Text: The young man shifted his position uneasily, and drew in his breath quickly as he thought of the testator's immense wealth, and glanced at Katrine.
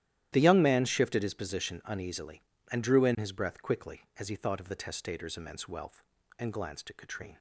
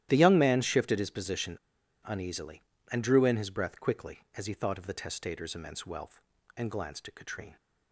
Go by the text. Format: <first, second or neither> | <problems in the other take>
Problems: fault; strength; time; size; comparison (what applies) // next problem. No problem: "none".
first | starts louder than the rest; strong; until 1.1 s; 13 dB; strong in the first // pauses between "position" and "uneasily"; noticeable; at 1.5 s; 0.49 s long